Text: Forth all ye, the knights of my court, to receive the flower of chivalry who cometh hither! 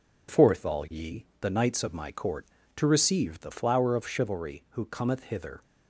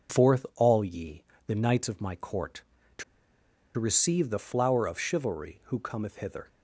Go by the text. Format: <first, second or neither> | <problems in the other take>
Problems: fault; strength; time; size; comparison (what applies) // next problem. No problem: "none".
first | pauses between "to" and "receive"; noticeable; at 3.0 s; 0.74 s long